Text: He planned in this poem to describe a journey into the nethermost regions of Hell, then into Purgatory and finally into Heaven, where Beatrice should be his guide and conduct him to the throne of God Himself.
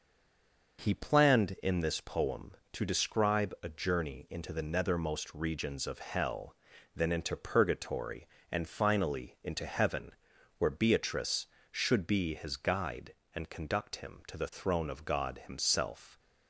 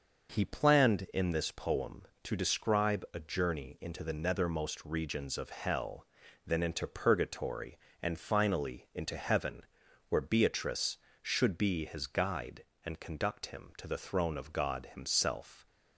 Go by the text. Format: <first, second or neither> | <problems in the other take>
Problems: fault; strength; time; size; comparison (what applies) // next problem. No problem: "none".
second | stays silent before the first word; slight; until 0.7 s; 0.7 s long